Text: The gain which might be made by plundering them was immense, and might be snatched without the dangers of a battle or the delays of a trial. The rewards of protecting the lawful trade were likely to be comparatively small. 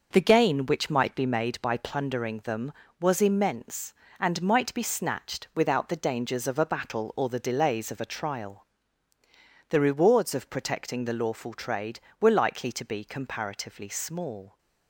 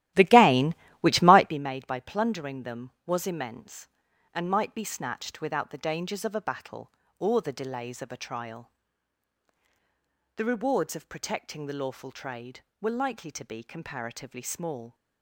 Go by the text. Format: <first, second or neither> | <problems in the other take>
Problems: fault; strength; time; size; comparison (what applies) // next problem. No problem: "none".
first | starts louder than the rest; strong; until 1.6 s; 14.5 dB